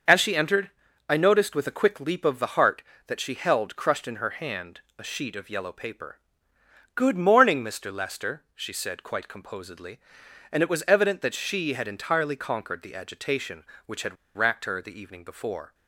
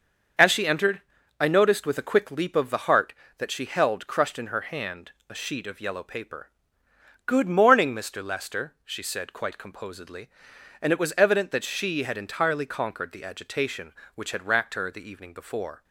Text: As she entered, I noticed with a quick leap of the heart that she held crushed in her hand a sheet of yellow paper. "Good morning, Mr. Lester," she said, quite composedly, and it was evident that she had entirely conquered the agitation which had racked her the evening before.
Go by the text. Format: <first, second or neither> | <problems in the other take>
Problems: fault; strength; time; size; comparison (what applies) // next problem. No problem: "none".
second | starts louder than the rest; until 1.4 s; 6.5 dB; also in the second // pauses between "hand" and "a"; slight; at 4.8 s; 0.16 s long; slight in the second // pauses between "had" and "racked"; slight; at 14.1 s; 0.20 s long